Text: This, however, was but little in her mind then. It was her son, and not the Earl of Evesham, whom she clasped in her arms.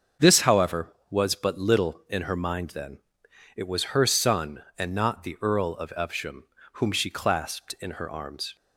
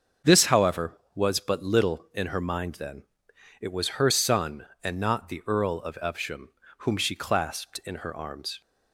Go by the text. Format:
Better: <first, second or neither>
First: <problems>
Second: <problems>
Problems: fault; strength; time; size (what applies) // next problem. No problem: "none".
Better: neither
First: starts louder than the rest; until 1.3 s; 6.5 dB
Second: starts louder than the rest; until 1.4 s; 6.5 dB